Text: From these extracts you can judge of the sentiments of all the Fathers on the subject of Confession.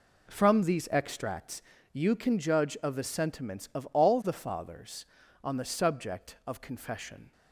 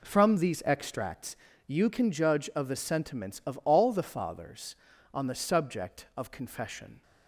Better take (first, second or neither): neither